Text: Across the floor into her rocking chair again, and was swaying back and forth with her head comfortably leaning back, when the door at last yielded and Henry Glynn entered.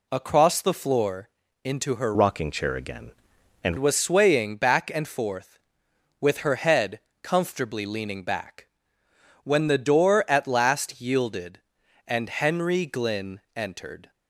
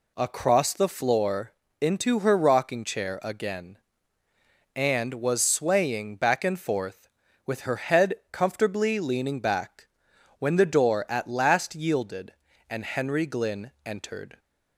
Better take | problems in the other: second | pauses between "floor" and "into"; slight; at 1.2 s; 0.36 s long; slight in the second // changes voice from "rocking" to "and"; from 2.1 to 3.7 s; 1.6 s long // pauses between "head" and "comfortably"; slight; at 7.0 s; 0.22 s long; slight in the second

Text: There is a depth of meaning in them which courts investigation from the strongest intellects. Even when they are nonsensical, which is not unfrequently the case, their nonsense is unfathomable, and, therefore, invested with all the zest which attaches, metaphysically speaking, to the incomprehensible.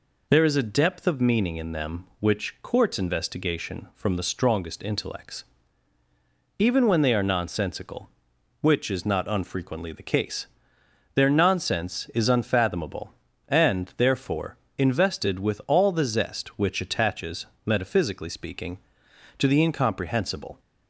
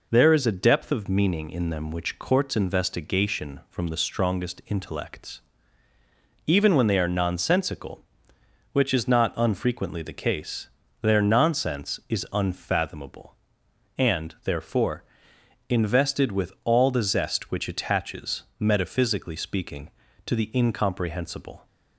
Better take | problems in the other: neither | none

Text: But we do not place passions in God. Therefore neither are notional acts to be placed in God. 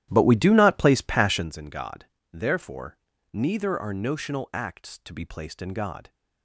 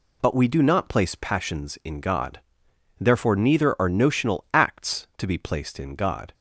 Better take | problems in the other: second | starts louder than the rest; strong; until 1.5 s; 13.5 dB // pauses between "Therefore" and "neither"; slight; at 2.9 s; 0.34 s long

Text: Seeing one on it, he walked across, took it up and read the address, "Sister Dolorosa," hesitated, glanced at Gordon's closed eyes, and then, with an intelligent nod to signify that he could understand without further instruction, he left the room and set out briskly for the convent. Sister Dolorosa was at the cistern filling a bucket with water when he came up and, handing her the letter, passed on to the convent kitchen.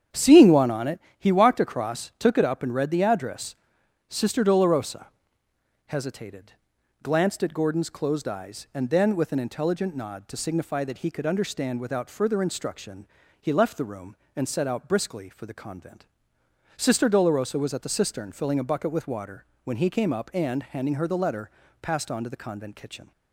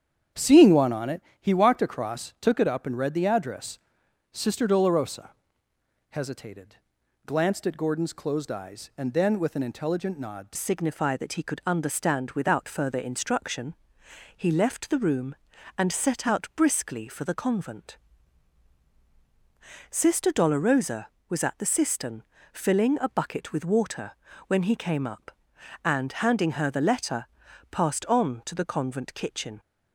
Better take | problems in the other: first | starts louder than the rest; strong; until 1.5 s; 8.5 dB; strong in the first // changes voice at "signify"; from 10.5 s on; 19.0 s long // pauses between "cistern" and "filling"; slight; at 22.2 s; 0.30 s long // pauses between "water" and "when"; slight; at 24.1 s; 0.34 s long; slight in the first

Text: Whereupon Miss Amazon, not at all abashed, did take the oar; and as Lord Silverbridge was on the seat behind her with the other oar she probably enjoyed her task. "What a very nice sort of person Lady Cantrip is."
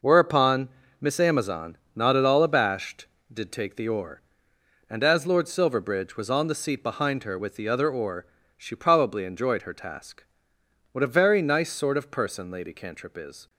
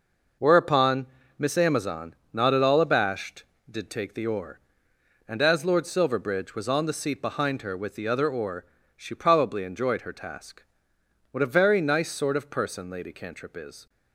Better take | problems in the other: neither | pauses between "Whereupon" and "Miss"; slight; the same in both // pauses between "oar" and "she"; slight; the same in both

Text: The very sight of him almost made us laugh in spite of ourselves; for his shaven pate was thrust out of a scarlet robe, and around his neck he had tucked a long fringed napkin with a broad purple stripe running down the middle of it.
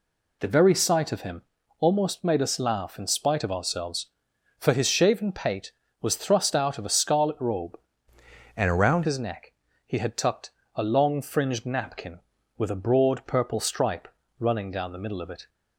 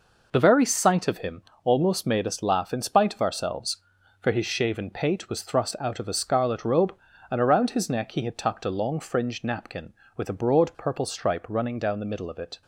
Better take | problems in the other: second | pauses between "him" and "almost"; slight; at 1.4 s; 0.36 s long; slight in the second // changes voice from "and" to "around"; from 8.5 to 9.0 s; 0.5 s long // pauses between "neck" and "he"; slight; at 9.5 s; 0.32 s long // pauses between "tucked" and "a"; slight; at 10.5 s; 0.22 s long // pauses between "stripe" and "running"; slight; at 14.0 s; 0.30 s long

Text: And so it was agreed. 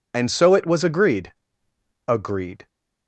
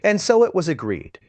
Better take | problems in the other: second | says "agreed" twice; at 2.0 s

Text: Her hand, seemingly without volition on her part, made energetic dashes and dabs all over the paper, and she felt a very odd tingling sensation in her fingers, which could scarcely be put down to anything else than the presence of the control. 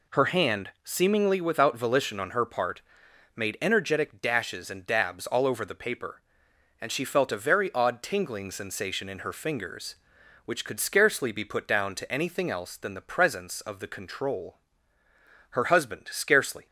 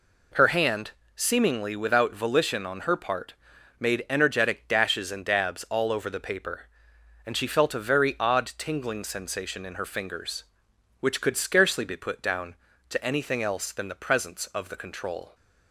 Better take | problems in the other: second | goes on to say "Her husband scarcely"; noticeable; from 15.5 s on; 1.1 s long

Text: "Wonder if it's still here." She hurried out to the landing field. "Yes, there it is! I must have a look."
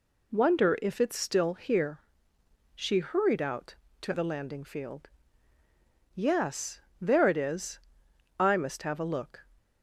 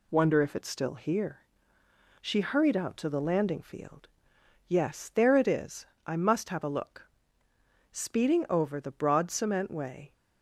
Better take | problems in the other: first | goes on to say "Speeding over the broad cement way"; strong; from 7.9 s on; 2.2 s long

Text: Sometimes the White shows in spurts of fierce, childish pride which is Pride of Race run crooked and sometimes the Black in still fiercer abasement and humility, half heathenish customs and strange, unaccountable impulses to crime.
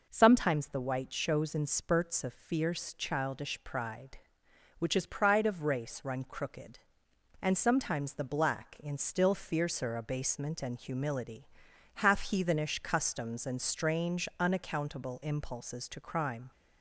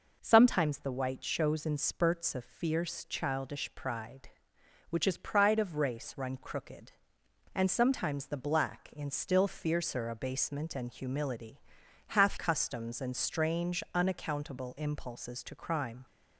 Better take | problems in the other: first | skips "heathenish"; at 12.3 s

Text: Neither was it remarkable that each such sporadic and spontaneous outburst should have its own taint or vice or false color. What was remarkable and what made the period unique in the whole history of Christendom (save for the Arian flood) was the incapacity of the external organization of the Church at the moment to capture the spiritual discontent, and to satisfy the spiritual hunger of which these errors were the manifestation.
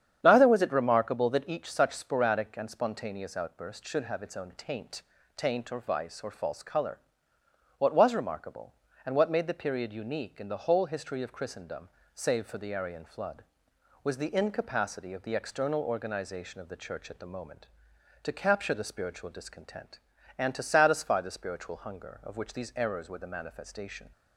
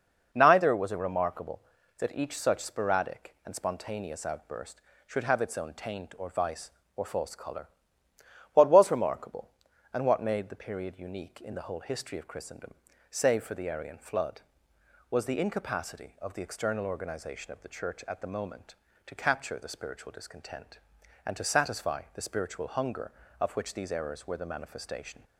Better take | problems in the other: second | starts louder than the rest; strong; until 1.2 s; 9 dB // says "taint" twice; at 5.3 s

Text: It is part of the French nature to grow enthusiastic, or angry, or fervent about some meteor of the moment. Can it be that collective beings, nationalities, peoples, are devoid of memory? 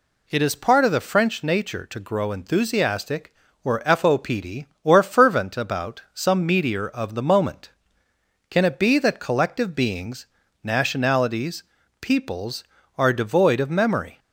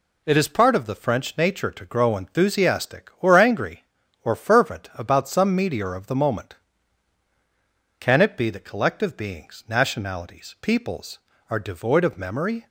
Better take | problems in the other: second | says "fopd" for "angry"; at 3.8 s

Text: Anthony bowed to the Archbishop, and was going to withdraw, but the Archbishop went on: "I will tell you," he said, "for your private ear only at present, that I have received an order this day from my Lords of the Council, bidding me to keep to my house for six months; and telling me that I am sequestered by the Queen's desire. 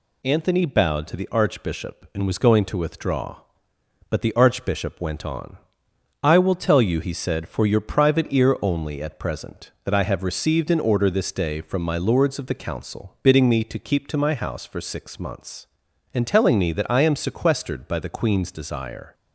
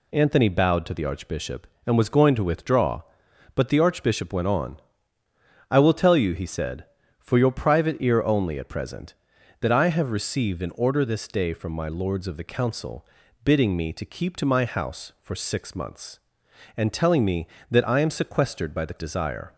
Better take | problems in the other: first | skips "Queen's"; at 18.9 s

